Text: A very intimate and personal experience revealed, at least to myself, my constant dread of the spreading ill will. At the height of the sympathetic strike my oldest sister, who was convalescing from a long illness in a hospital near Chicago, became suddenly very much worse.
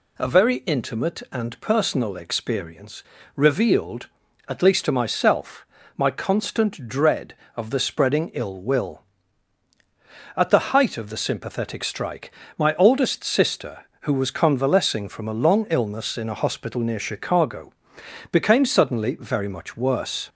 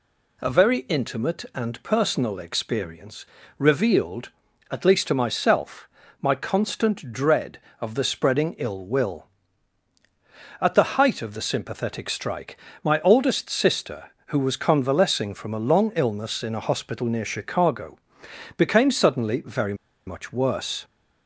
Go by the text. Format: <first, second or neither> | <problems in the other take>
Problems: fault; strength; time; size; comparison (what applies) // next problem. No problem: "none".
first | pauses between "experience" and "revealed"; slight; at 3.2 s; 0.32 s long; slight in the first // pauses between "strike" and "my"; slight; at 12.5 s; 0.28 s long; slight in the first // pauses between "very" and "much"; slight; at 19.7 s; 0.32 s long